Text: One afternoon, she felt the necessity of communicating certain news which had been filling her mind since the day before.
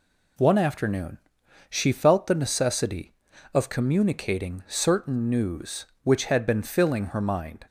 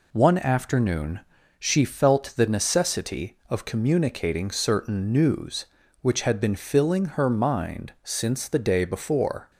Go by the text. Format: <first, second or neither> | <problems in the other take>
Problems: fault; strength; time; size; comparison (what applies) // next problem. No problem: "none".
second | stops before "since the day before"; at 7.6 s